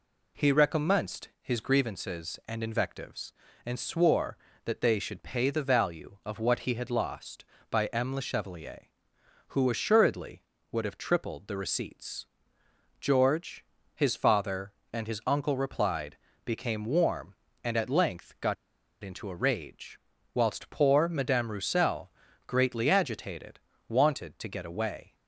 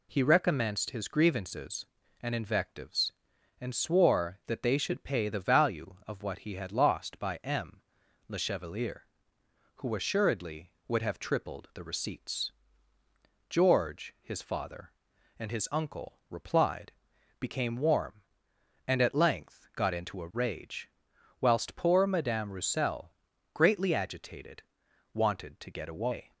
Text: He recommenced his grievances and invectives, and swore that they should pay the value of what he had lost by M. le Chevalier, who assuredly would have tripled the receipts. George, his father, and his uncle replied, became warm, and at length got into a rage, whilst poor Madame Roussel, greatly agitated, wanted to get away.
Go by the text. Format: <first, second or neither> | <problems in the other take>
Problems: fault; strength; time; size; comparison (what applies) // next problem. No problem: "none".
second | pauses between "got" and "into"; noticeable; at 18.5 s; 0.48 s long